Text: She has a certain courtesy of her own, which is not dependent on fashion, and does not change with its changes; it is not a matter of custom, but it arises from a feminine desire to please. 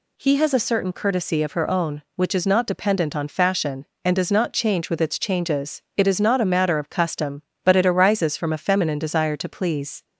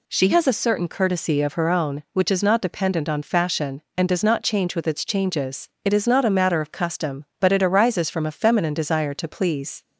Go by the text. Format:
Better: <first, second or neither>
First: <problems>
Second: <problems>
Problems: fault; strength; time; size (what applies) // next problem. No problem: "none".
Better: second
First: says "He" for "She"; at 0.1 s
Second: none